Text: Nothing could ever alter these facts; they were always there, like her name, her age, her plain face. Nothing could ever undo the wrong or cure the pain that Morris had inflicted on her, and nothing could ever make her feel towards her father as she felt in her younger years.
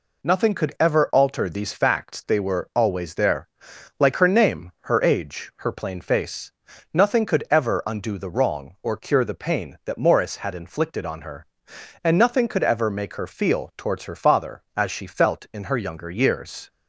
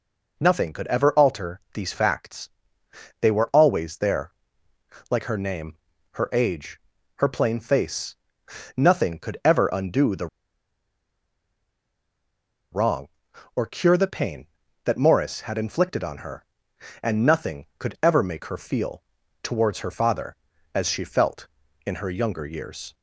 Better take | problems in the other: first | pauses between "the" and "wrong"; strong; at 10.2 s; 2.4 s long // pauses between "feel" and "towards"; at 19.0 s; 0.40 s long

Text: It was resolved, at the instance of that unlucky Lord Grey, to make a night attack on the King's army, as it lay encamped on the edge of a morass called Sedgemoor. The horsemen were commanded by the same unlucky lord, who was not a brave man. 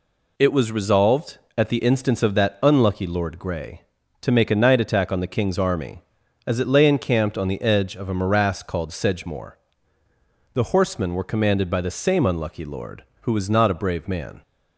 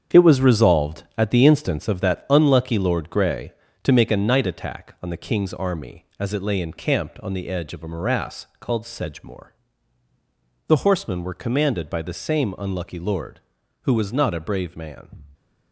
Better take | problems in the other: first | gets quieter; strong; throughout; 9 dB

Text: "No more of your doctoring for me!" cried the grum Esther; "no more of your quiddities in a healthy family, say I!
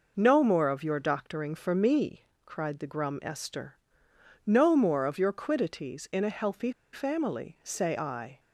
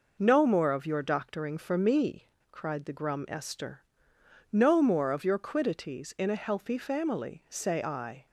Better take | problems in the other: second | pauses between "healthy" and "family"; slight; at 6.7 s; 0.20 s long

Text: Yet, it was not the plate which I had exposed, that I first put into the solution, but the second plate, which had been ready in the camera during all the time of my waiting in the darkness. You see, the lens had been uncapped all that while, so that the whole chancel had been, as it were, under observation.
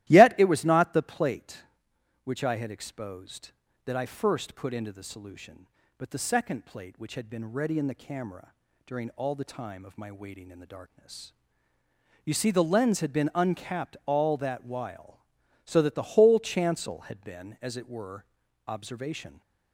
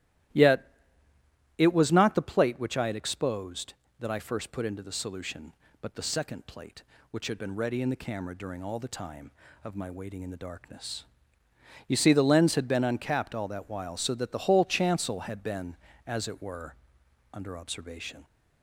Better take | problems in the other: second | starts louder than the rest; strong; until 1.1 s; 15.5 dB; strong in the second // pauses between "camera" and "during"; slight; at 8.5 s; 0.32 s long // skips "under"; at 18.4 s

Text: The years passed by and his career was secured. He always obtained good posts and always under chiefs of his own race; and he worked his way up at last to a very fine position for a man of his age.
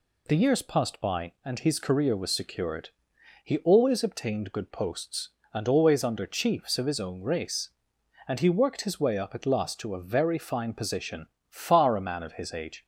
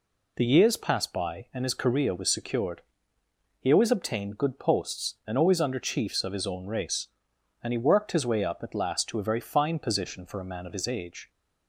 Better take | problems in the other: second | says "far" for "for"; at 11.4 s

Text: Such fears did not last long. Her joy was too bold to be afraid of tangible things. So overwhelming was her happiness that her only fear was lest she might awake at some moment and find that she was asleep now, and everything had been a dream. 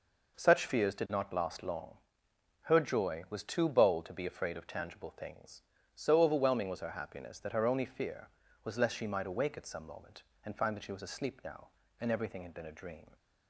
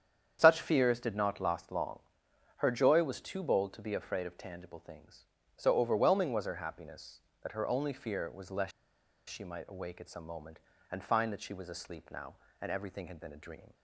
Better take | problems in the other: first | starts louder than the rest; strong; until 1.4 s; 8.5 dB // pauses between "lest" and "she"; noticeable; at 8.7 s; 0.58 s long

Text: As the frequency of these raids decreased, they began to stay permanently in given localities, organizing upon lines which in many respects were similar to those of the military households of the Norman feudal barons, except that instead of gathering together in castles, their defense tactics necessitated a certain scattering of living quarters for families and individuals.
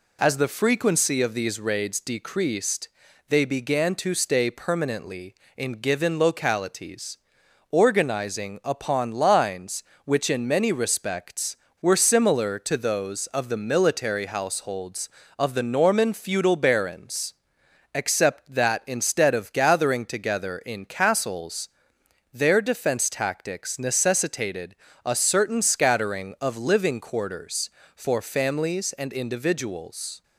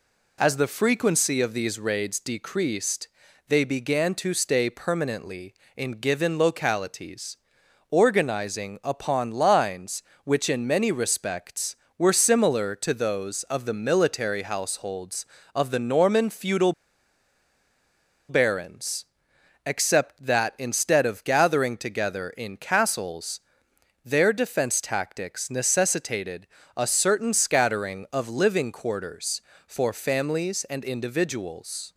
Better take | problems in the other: first | pauses between "feudal" and "barons"; strong; at 16.7 s; 1.5 s long // pauses between "necessitated" and "a"; slight; at 26.4 s; 0.30 s long; slight in the first

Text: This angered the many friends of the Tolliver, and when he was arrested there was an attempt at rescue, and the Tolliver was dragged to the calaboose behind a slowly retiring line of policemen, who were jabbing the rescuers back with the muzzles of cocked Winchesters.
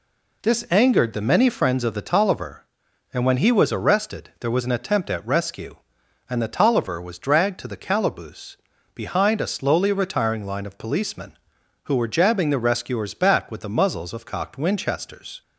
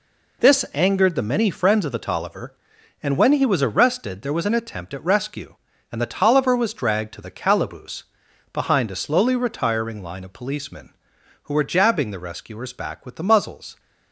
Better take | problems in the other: first | pauses between "calaboose" and "behind"; noticeable; at 8.0 s; 0.48 s long; also in the first // stops before "of cocked Winchesters"; at 13.7 s

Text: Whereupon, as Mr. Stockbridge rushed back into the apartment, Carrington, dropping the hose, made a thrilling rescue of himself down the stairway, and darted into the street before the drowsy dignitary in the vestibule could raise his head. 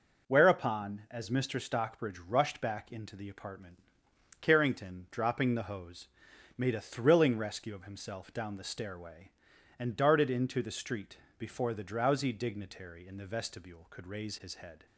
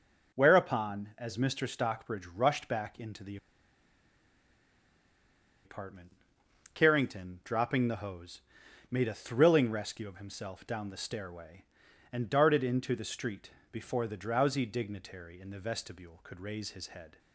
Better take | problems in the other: first | pauses between "the" and "apartment"; strong; at 3.3 s; 2.2 s long // pauses between "street" and "before"; slight; at 13.5 s; 0.20 s long; slight in the first

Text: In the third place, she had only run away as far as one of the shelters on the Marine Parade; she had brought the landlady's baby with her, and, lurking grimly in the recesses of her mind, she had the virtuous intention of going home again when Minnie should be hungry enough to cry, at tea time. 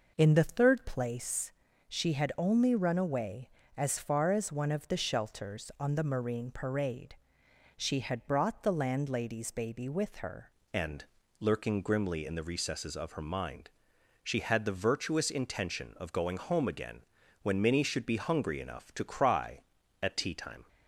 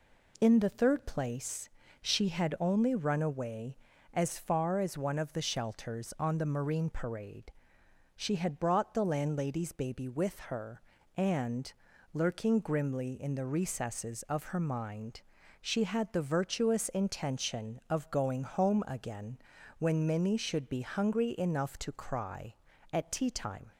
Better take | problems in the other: second | changes voice at "and"; from 10.7 s on; 9.9 s long // pauses between "again" and "when"; slight; at 17.0 s; 0.36 s long; also in the second

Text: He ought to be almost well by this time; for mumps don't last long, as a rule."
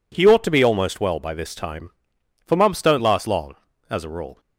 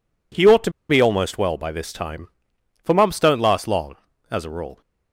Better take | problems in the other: first | pauses between "to" and "be"; slight; at 0.7 s; 0.18 s long

